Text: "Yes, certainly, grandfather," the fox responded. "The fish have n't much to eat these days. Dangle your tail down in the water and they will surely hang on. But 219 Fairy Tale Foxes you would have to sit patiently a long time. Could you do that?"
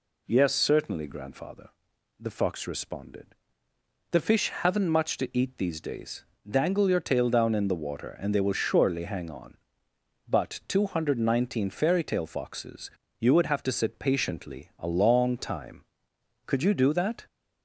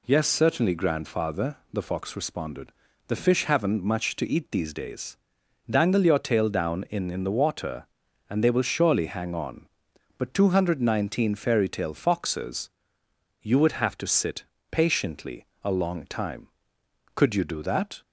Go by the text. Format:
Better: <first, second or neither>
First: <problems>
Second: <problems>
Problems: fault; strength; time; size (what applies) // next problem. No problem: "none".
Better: first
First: pauses between "Foxes" and "you"; slight; at 12.9 s; 0.30 s long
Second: says "in" twice; at 7.1 s // pauses between "Foxes" and "you"; noticeable; at 12.7 s; 0.72 s long // pauses between "sit" and "patiently"; slight; at 14.4 s; 0.26 s long // pauses between "patiently" and "a"; slight; at 15.4 s; 0.18 s long